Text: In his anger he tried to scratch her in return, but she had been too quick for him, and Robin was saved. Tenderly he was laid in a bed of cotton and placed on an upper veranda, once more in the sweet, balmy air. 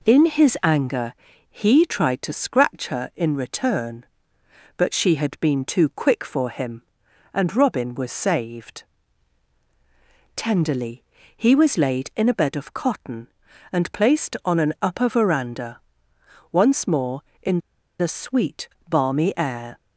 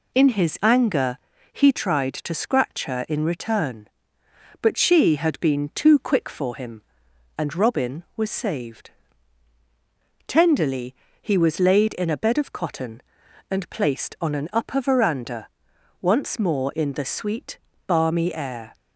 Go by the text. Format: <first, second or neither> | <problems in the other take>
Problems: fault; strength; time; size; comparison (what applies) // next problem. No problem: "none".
second | pauses between "anger" and "he"; slight; at 1.1 s; 0.34 s long; slight in the second // pauses between "Tenderly" and "he"; slight; at 11.0 s; 0.32 s long; slight in the second // pauses between "in" and "the"; at 17.5 s; 0.41 s long